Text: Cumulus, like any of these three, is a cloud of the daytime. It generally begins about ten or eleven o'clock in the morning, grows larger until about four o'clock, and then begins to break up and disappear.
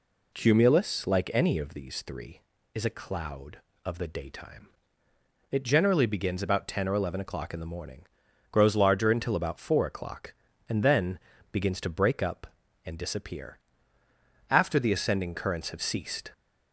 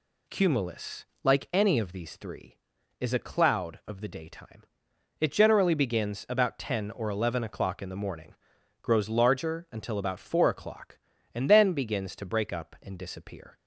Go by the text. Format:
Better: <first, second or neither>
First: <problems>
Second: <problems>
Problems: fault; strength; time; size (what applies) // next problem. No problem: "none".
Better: second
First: pauses between "then" and "begins"; slight; at 11.1 s; 0.34 s long // goes on to say "After the ascending currents have ceased"; strong; from 14.4 s on; 1.8 s long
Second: none